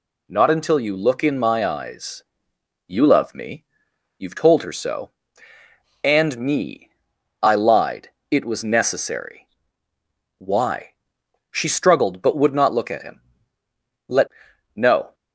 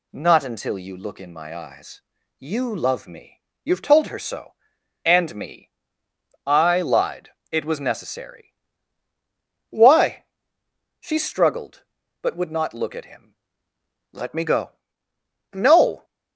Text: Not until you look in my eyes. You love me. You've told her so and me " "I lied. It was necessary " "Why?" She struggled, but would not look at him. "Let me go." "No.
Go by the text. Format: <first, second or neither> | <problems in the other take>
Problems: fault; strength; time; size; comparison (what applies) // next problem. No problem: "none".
second | skips "me go"; at 14.5 s